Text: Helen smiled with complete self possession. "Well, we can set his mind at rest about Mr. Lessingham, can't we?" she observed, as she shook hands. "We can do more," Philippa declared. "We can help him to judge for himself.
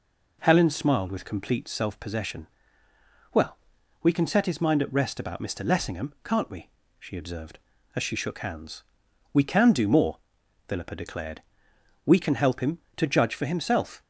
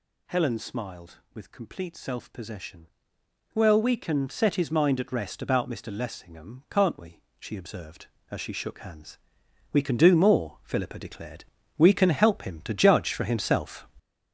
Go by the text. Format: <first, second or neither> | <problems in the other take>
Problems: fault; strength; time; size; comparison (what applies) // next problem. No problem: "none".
first | gets louder; throughout; 6.5 dB